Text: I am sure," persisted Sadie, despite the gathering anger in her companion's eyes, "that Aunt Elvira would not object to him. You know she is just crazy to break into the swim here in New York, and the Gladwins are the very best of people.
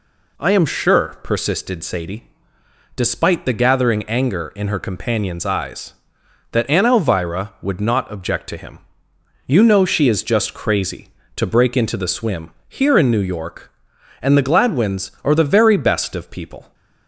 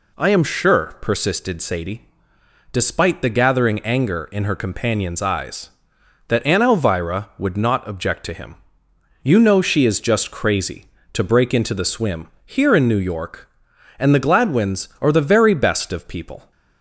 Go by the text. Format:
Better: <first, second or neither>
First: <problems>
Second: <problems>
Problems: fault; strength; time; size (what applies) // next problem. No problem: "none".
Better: neither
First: pauses between "swim" and "here"; slight; at 12.4 s; 0.18 s long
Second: pauses between "swim" and "here"; slight; at 12.2 s; 0.18 s long